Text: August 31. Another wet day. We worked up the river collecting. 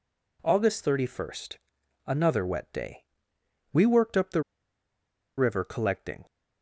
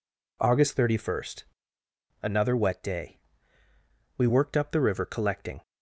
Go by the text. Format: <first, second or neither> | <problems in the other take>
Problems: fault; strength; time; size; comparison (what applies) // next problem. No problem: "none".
second | pauses between "the" and "river"; noticeable; at 4.4 s; 0.97 s long